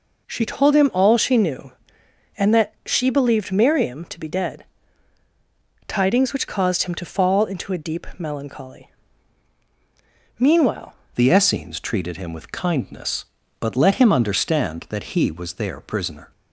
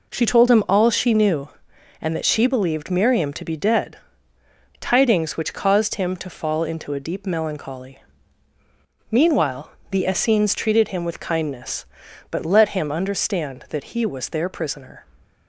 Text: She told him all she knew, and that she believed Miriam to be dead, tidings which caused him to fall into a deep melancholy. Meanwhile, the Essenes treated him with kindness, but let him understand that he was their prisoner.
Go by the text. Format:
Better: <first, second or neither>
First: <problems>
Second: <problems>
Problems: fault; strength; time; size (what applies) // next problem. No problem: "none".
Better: second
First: changes voice at "the"; from 11.1 s on; 5.2 s long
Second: none